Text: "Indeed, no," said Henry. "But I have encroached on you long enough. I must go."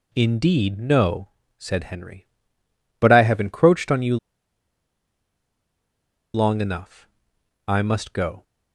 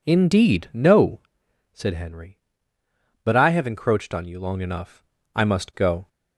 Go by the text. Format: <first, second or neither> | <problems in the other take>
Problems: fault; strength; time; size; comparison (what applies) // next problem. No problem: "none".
second | pauses between "you" and "long"; strong; at 4.1 s; 2.1 s long